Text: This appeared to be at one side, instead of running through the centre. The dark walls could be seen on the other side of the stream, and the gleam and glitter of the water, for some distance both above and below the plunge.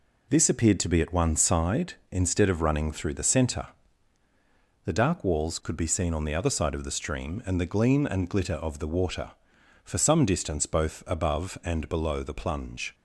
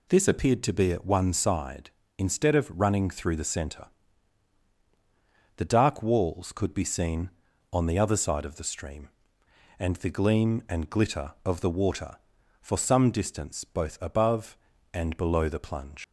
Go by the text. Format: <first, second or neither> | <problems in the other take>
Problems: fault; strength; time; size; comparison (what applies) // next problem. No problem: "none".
first | leaves "plunge" unfinished; at 16.0 s; 85 ms